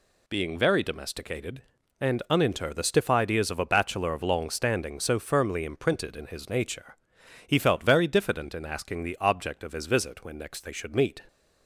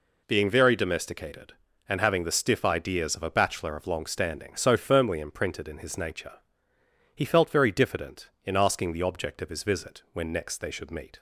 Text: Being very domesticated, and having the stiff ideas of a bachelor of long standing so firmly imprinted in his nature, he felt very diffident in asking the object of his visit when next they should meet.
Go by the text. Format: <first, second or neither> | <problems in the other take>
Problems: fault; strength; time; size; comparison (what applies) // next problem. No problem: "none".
second | says "uninter" for "having"; at 2.2 s